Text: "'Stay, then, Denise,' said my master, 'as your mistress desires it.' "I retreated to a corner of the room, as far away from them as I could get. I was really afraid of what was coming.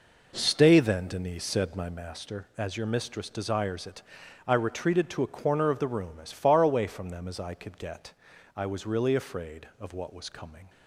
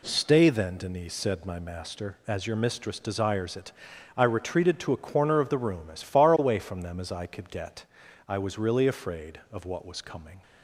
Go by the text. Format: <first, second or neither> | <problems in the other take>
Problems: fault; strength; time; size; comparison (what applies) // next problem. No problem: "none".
second | starts louder than the rest; noticeable; until 2.0 s; 4.5 dB